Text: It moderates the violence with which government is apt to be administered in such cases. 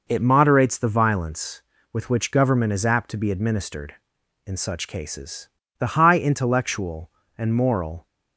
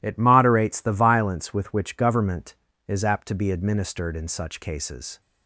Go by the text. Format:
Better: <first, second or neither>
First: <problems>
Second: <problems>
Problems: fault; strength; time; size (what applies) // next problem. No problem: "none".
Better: second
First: goes on to say "The high intellectual and moral"; strong; from 5.7 s on; 2.2 s long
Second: none